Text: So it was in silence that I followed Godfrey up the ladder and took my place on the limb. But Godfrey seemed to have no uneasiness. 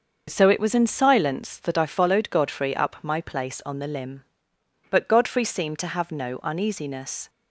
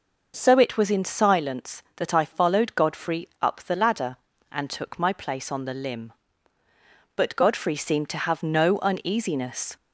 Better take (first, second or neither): second